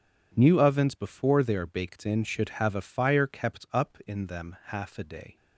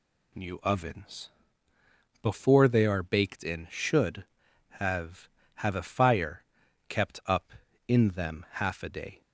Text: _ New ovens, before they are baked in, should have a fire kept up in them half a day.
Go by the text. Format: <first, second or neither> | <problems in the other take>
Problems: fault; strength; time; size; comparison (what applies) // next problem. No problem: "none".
first | says "have" twice; at 5.5 s // pauses between "fire" and "kept"; at 6.4 s; 0.42 s long